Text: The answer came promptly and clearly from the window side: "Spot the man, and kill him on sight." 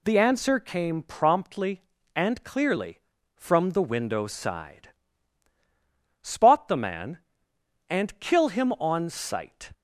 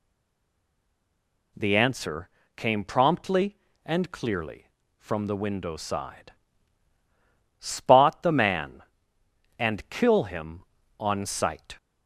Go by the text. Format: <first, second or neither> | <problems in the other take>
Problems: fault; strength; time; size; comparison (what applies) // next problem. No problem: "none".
first | stays silent before the first word; noticeable; until 1.5 s; 1.5 s long // pauses between "answer" and "came"; slight; at 2.2 s; 0.28 s long